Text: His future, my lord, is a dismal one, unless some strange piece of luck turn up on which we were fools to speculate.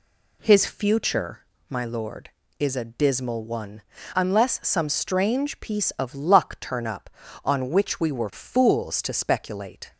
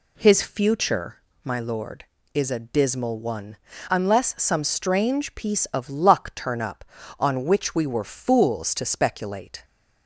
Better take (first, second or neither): neither